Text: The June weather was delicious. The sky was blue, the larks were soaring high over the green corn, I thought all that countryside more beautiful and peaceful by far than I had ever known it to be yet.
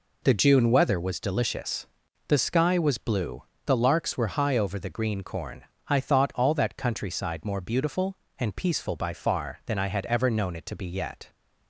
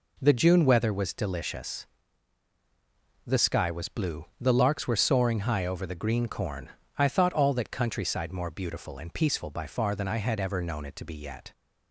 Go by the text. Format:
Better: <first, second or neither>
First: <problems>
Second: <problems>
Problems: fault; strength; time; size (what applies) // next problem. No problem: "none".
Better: second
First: skips "soaring"; at 4.3 s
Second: none